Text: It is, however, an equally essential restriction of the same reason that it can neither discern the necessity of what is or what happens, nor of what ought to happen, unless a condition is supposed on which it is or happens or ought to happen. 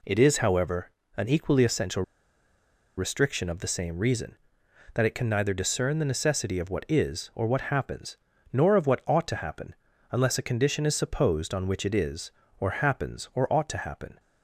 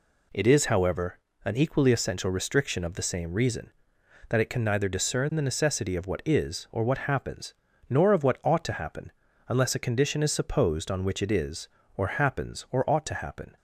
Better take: second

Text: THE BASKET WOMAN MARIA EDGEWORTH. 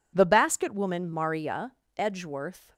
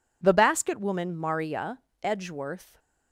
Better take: neither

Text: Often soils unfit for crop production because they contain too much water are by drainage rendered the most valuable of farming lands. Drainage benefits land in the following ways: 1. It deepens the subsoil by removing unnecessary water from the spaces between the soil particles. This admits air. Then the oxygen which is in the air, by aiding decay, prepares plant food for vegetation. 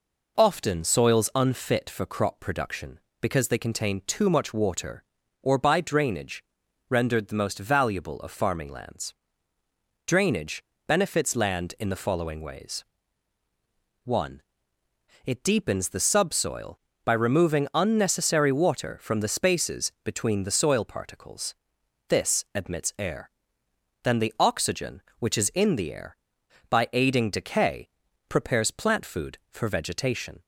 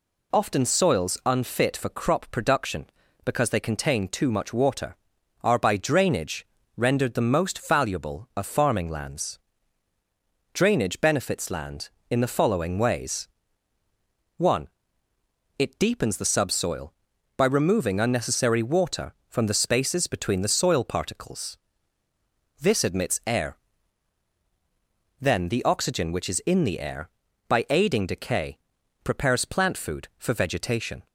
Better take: second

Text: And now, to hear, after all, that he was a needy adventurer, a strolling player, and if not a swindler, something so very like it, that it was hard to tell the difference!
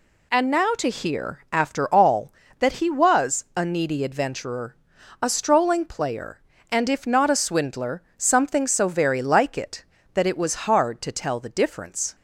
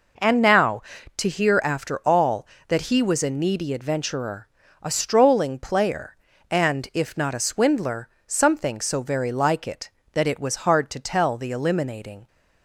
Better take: first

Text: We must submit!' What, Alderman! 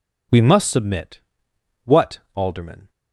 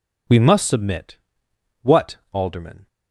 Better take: neither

